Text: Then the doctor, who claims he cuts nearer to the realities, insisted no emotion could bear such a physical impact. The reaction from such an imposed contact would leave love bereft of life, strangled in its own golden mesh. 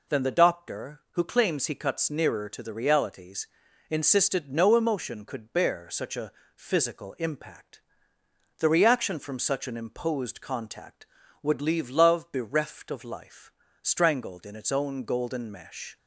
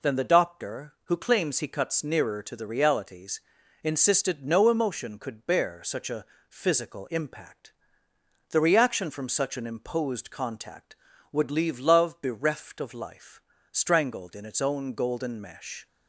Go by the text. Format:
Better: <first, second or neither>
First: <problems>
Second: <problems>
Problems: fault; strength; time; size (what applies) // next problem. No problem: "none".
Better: neither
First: pauses between "a" and "physical"; slight; at 6.3 s; 0.24 s long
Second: pauses between "a" and "physical"; slight; at 6.2 s; 0.24 s long